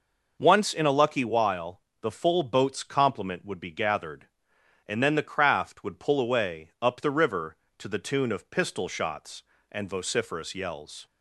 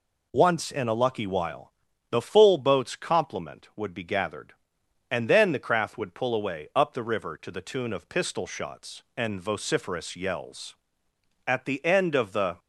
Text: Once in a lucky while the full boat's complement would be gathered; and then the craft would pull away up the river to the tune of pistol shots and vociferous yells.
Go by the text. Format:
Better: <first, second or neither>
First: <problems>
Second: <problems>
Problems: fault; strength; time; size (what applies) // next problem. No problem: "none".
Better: first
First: pauses between "while" and "the"; slight; at 1.7 s; 0.22 s long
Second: pauses between "while" and "the"; at 1.7 s; 0.40 s long // goes on to say "At the end of the"; noticeable; from 11.4 s on; 1.1 s long